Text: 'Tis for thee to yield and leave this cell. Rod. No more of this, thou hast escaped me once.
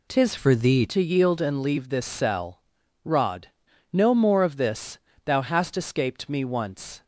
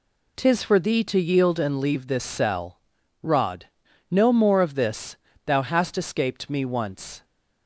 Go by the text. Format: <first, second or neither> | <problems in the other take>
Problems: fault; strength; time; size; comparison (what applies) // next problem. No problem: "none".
second | changes voice from "for" to "thee"; from 0.3 to 0.8 s; 0.5 s long